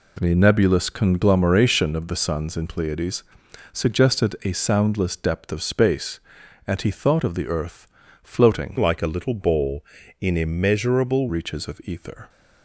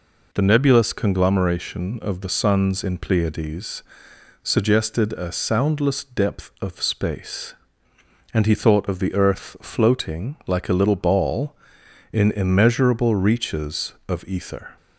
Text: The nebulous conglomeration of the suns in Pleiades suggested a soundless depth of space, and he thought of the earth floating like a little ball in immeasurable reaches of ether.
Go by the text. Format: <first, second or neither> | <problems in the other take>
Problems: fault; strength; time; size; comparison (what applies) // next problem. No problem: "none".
second | pauses between "Pleiades" and "suggested"; noticeable; at 3.2 s; 0.50 s long; noticeable in the second // pauses between "earth" and "floating"; at 7.8 s; 0.38 s long // changes voice from "like" to "immeasurable"; from 8.7 to 11.2 s; 2.5 s long